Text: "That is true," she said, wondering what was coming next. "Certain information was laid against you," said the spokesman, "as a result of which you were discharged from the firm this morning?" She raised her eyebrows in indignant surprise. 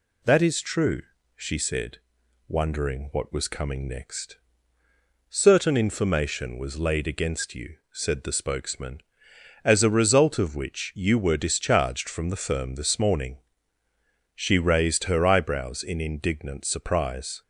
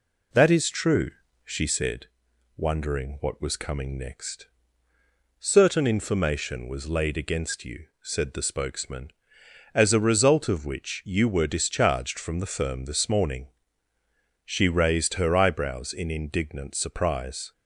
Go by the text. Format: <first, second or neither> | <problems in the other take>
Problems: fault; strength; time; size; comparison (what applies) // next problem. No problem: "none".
first | starts louder than the rest; slight; until 2.1 s; 3 dB